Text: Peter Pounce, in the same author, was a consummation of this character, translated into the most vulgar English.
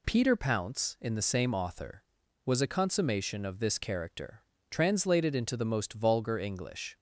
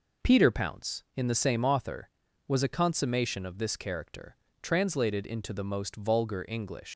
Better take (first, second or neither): first